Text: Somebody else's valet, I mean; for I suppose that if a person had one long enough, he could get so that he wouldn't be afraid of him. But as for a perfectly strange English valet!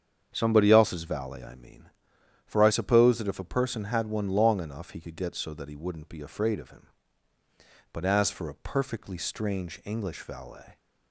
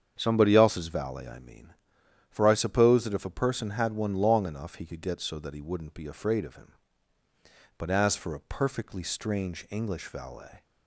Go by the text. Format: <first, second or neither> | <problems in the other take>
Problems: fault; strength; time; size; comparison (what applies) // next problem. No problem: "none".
neither | starts louder than the rest; strong; the same in both